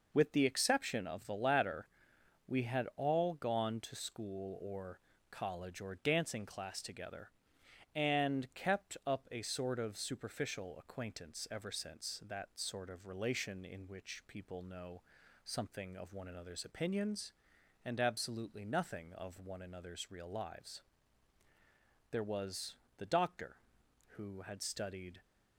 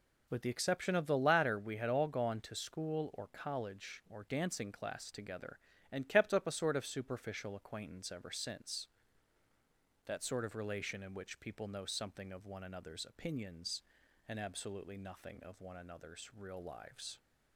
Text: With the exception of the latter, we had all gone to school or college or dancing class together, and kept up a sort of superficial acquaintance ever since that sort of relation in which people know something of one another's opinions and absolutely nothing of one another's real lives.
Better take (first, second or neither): second